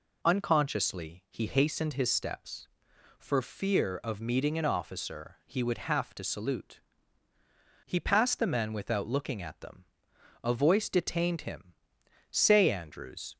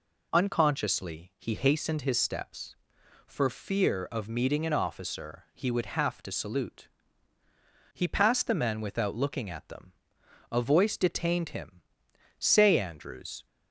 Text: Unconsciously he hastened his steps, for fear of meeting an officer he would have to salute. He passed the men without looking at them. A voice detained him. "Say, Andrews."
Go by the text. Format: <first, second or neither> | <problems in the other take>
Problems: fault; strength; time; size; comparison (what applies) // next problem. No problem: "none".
neither | none